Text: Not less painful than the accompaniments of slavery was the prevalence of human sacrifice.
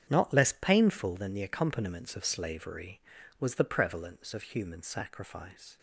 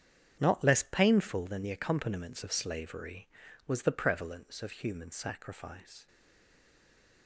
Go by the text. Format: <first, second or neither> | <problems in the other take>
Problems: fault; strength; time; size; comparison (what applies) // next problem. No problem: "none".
first | starts louder than the rest; strong; until 1.4 s; 8.5 dB; strong in the first // stays silent after the last word; noticeable; from 6.0 s on; 1.2 s long